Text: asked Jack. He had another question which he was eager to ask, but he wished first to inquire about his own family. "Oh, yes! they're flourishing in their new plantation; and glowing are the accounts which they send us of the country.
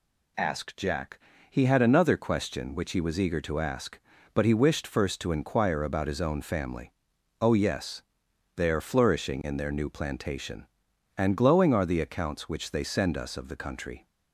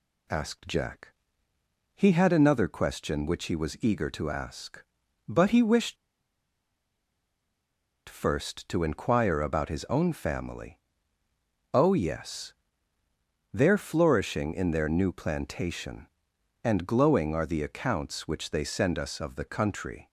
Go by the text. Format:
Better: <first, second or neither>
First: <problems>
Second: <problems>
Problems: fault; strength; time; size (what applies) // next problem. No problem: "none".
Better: first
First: none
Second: pauses between "wished" and "first"; strong; at 5.9 s; 2.1 s long